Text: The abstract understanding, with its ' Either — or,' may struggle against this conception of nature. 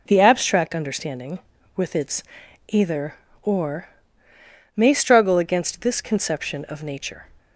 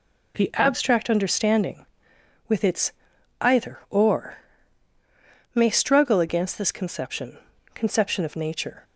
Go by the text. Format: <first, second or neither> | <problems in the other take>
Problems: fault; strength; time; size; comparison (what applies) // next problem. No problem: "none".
first | says "conception" twice; at 7.7 s